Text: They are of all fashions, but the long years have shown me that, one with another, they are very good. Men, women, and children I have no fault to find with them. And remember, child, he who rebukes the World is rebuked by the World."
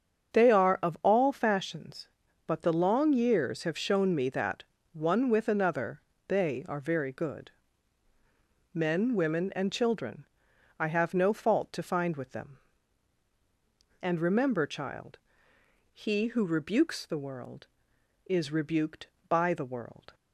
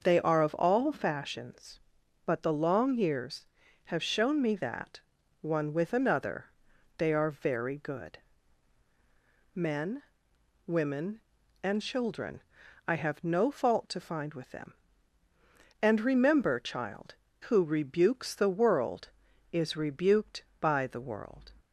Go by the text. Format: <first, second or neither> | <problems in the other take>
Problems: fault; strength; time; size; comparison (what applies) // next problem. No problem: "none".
first | starts louder than the rest; until 1.0 s; 6 dB; strong in the first // pauses between "children" and "I"; noticeable; at 12.3 s; 0.48 s long; noticeable in the first // skips "he"; at 17.2 s